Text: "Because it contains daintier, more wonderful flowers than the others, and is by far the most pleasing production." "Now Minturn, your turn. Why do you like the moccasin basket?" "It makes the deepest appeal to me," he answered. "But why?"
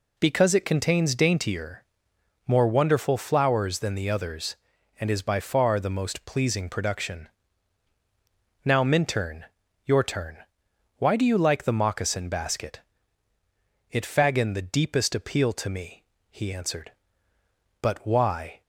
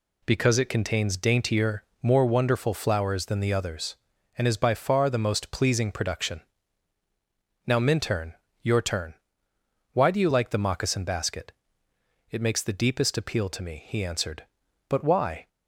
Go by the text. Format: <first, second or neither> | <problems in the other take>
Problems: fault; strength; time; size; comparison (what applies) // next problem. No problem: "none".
second | says "faggin" for "makes"; at 14.0 s